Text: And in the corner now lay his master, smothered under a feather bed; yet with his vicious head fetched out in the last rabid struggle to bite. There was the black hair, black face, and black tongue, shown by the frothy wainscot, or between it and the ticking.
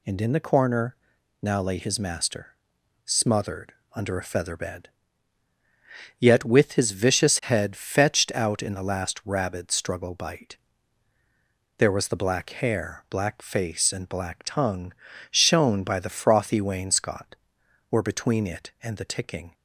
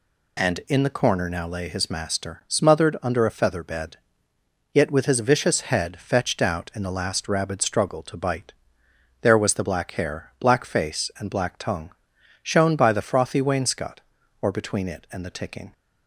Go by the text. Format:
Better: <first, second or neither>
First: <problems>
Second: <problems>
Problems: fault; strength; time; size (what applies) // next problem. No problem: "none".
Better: second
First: pauses between "corner" and "now"; noticeable; at 0.9 s; 0.48 s long // pauses between "smothered" and "under"; slight; at 3.7 s; 0.22 s long // skips "to"; at 10.1 s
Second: none